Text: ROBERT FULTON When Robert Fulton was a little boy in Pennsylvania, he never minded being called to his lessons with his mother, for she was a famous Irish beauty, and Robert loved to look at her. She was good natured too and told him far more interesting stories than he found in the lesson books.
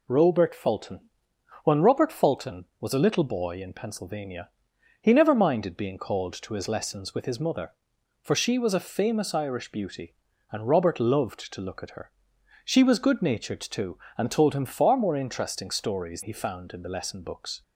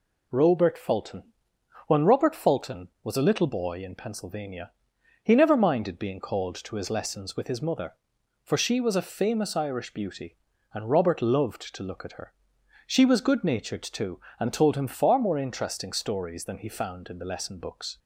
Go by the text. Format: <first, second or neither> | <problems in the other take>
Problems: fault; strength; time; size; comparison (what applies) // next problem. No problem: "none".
second | pauses between "FULTON" and "When"; noticeable; at 1.0 s; 0.56 s long; noticeable in the second // skips "than"; at 16.2 s